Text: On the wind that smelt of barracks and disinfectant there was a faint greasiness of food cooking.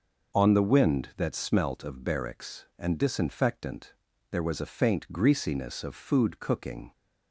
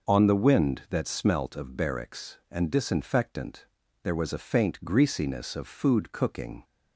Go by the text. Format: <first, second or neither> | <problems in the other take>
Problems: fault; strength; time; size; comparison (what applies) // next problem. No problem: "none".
neither | pauses between "disinfectant" and "there"; slight; the same in both